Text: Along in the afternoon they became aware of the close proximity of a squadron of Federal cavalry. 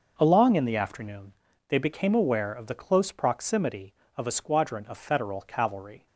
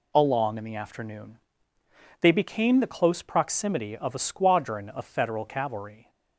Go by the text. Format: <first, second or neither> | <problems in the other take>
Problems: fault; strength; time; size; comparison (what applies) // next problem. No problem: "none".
first | pauses between "afternoon" and "they"; noticeable; at 1.3 s; 0.84 s long; slight in the first // skips "aware of"; at 2.7 s